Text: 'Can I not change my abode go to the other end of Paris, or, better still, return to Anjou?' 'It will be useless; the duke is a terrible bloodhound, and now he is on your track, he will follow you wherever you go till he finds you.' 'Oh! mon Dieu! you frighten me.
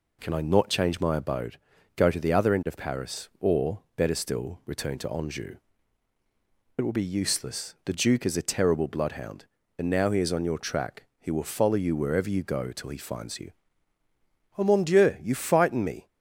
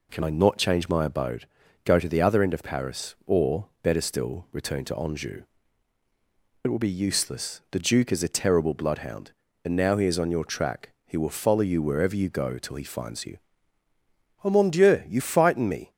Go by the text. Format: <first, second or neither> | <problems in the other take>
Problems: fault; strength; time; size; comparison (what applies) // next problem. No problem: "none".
neither | pauses between "abode" and "go"; the same in both